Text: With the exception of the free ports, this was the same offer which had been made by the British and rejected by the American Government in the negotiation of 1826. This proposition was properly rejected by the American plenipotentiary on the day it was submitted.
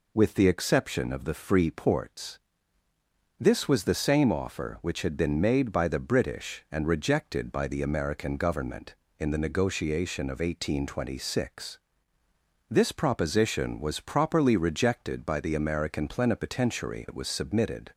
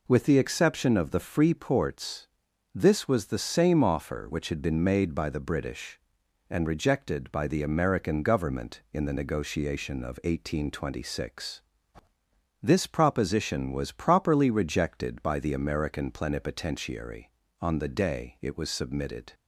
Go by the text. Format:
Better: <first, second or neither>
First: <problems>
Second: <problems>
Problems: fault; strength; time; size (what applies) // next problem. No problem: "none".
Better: second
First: skips "on the day"; at 17.0 s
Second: none